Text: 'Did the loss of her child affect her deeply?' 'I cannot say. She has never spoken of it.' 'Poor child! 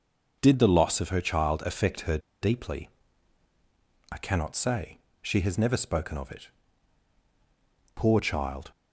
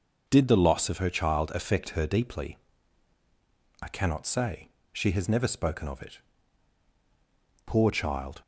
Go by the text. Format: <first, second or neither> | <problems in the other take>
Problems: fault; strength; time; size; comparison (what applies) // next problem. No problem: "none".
second | pauses between "her" and "deeply"; slight; at 2.1 s; 0.23 s long